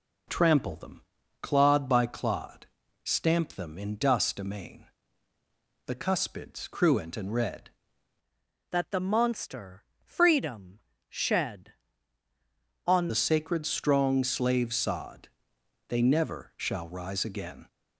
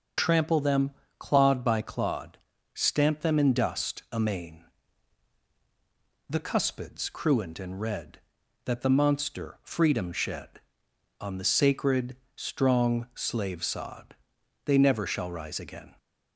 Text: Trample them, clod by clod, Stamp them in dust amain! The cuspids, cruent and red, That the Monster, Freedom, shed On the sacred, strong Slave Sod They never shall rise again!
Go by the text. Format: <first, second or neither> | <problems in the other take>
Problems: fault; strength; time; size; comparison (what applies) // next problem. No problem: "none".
second | changes voice from "That" to "On"; from 8.7 to 13.0 s; 4.3 s long // pauses between "Sod" and "They"; noticeable; at 15.2 s; 0.60 s long; noticeable in the second